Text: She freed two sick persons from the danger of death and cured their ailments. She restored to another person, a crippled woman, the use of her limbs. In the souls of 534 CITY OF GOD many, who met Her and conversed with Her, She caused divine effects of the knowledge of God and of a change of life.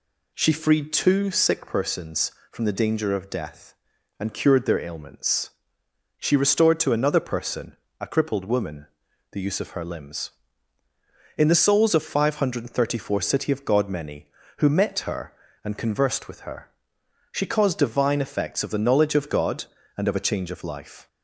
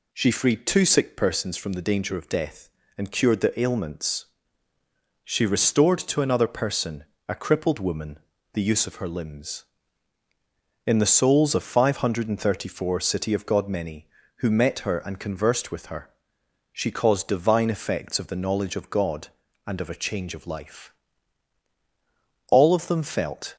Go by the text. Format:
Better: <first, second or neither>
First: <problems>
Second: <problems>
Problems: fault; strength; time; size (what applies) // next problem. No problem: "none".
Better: first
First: none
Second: goes on to say "All of them felt"; noticeable; from 22.4 s on; 1.0 s long